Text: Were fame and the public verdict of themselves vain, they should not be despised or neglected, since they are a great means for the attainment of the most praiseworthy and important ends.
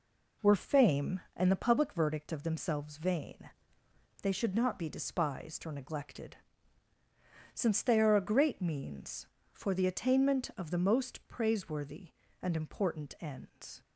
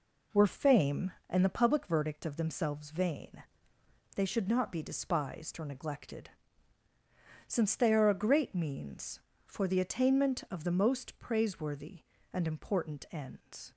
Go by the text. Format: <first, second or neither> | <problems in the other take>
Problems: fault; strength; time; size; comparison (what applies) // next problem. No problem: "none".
neither | none